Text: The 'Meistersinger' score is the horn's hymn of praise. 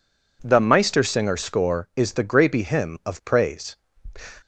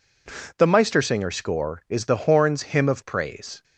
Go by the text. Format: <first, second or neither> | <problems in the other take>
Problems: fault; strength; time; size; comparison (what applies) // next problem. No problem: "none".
second | says "grapey" for "horn's"; at 2.2 s